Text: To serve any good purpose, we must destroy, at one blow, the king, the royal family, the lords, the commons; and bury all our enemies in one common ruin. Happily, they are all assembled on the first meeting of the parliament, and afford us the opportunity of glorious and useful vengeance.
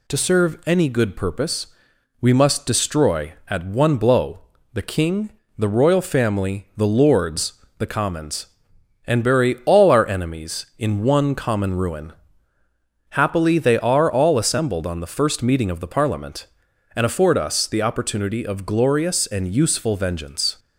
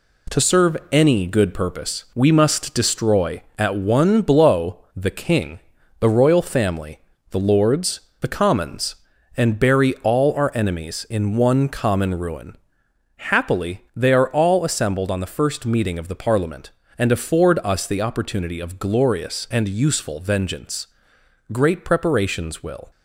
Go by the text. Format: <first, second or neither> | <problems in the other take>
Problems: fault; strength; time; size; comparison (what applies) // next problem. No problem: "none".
first | pauses between "serve" and "any"; slight; at 0.7 s; 0.16 s long // goes on to say "Great preparations will"; from 21.5 s on; 1.3 s long